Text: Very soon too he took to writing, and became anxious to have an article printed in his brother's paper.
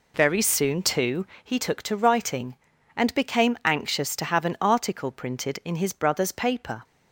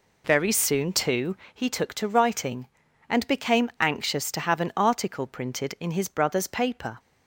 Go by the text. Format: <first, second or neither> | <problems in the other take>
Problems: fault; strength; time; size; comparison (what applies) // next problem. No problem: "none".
neither | pauses between "too" and "he"; slight; the same in both